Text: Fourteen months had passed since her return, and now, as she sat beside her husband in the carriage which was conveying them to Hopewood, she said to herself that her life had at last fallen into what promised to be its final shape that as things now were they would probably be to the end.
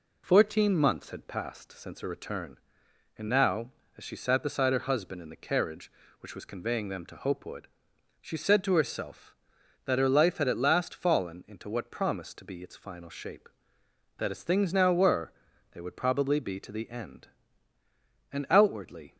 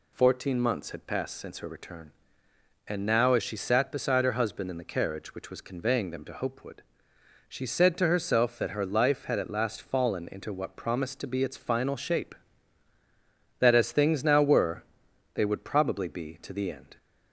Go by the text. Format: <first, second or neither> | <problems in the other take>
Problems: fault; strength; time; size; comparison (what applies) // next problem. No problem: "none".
second | pauses between "were" and "they"; at 15.3 s; 0.40 s long; noticeable in the second // goes on to say "And outwardly"; noticeable; from 18.3 s on; 0.84 s long